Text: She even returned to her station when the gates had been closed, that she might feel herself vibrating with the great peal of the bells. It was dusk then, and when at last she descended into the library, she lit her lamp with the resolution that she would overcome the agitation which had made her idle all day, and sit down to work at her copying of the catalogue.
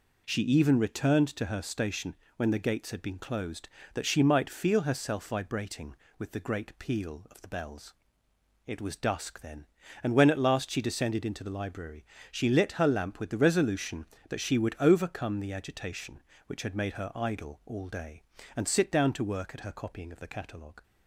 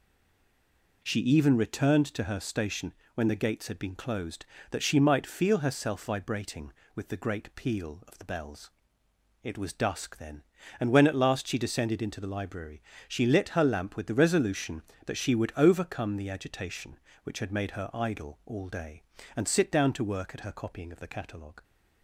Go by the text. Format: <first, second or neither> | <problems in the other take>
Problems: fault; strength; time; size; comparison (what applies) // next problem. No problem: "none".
first | stays silent before the first word; until 1.0 s; 1.0 s long // pauses between "station" and "when"; slight; at 2.9 s; 0.22 s long; slight in the first